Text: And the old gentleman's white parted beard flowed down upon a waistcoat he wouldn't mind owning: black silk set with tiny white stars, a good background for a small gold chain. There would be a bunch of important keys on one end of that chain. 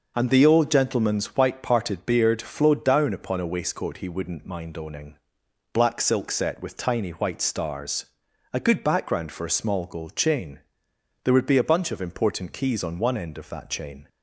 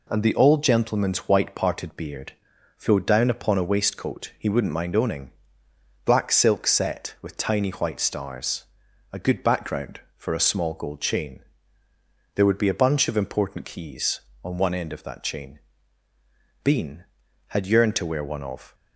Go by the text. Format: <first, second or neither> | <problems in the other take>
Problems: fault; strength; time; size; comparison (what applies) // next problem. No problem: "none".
first | pauses between "beard" and "flowed"; noticeable; at 2.3 s; 0.46 s long // goes on to say "Bean had yearned to wear one of"; strong; from 16.6 s on; 2.1 s long